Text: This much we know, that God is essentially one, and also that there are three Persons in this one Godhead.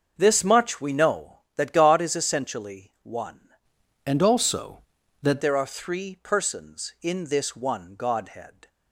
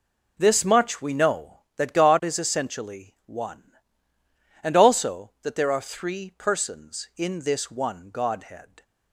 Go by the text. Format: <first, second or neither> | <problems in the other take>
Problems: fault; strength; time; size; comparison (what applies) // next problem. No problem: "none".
second | starts louder than the rest; until 1.1 s; 6.5 dB // changes voice from "and" to "that"; from 4.0 to 5.4 s; 1.4 s long